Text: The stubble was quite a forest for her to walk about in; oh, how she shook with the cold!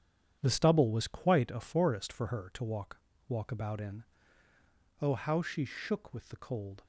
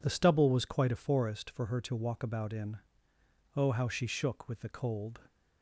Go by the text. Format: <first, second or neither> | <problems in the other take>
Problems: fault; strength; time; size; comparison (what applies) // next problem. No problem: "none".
second | starts louder than the rest; strong; until 1.4 s; 9 dB // says "walk" twice; at 3.2 s